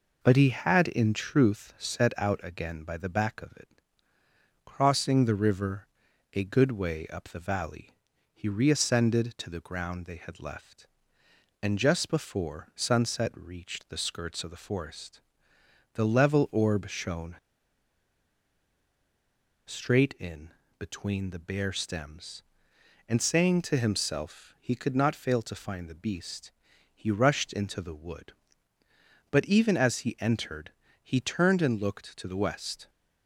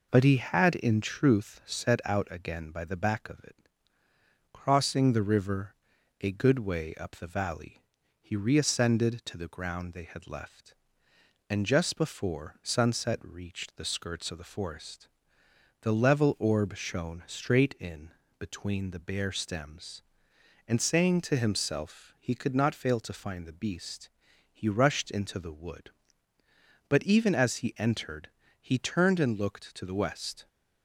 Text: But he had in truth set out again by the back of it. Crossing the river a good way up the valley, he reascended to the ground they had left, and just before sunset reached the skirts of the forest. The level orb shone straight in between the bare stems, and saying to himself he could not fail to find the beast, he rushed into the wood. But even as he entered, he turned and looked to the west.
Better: second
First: pauses between "river" and "a"; noticeable; at 5.8 s; 0.46 s long // pauses between "shone" and "straight"; strong; at 17.3 s; 2.3 s long // pauses between "in" and "between"; slight; at 20.4 s; 0.28 s long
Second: pauses between "river" and "a"; noticeable; at 5.7 s; 0.46 s long // pauses between "in" and "between"; slight; at 18.0 s; 0.28 s long

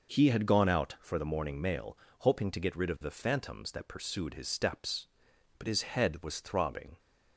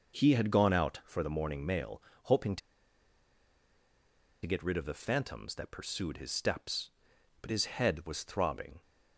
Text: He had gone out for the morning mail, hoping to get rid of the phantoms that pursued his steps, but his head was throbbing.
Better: first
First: none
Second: pauses between "to" and "get"; strong; at 2.6 s; 1.8 s long

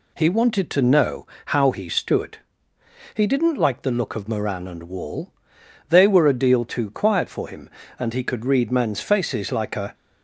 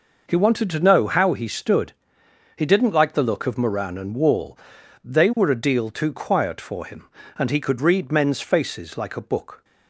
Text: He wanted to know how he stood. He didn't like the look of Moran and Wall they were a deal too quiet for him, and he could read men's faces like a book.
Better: second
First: pauses between "know" and "how"; slight; at 1.2 s; 0.20 s long // pauses between "Wall" and "they"; noticeable; at 5.3 s; 0.58 s long // stops before "book"; at 9.9 s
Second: pauses between "Wall" and "they"; noticeable; at 4.5 s; 0.52 s long

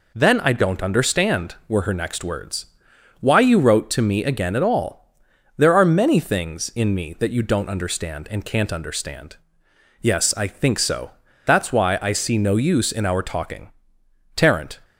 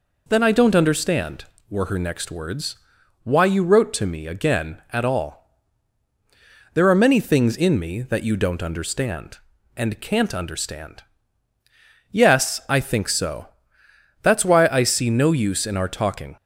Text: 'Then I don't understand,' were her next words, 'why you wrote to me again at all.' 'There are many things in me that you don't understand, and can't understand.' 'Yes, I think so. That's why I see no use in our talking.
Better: second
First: goes on to say "Tarrant"; slight; from 14.3 s on; 0.44 s long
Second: none

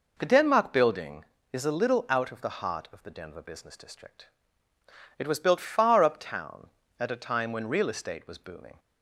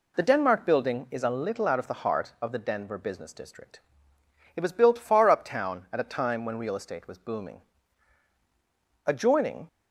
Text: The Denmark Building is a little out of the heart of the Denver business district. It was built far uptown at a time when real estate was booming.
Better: first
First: none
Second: goes on to say "Adjoining"; noticeable; from 9.0 s on; 0.62 s long

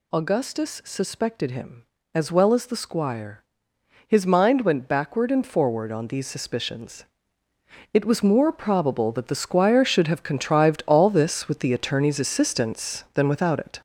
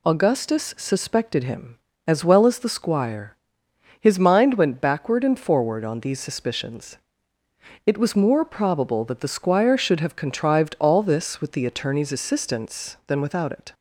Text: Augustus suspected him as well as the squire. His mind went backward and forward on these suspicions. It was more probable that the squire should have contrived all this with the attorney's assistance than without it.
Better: second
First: gets louder; throughout; 6 dB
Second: none

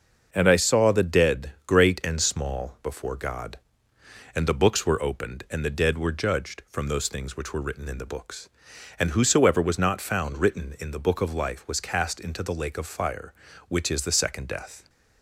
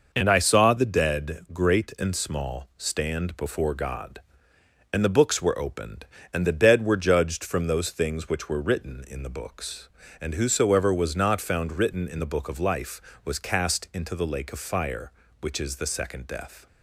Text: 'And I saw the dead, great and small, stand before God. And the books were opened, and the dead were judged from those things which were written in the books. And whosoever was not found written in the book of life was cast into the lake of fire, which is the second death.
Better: second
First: starts louder than the rest; until 1.3 s; 6 dB // skips "stand"; at 2.8 s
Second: none

